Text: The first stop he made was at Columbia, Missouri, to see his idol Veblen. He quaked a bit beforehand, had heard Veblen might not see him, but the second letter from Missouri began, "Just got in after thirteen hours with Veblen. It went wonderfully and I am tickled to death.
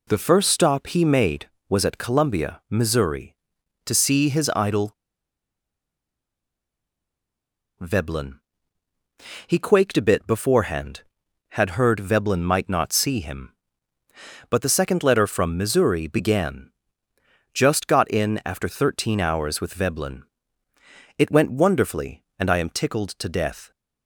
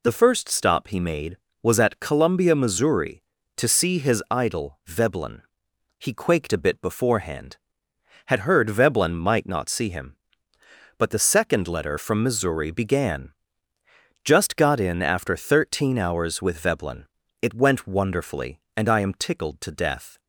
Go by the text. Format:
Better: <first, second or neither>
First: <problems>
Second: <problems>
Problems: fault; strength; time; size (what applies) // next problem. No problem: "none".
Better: second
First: pauses between "idol" and "Veblen"; strong; at 4.9 s; 2.8 s long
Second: none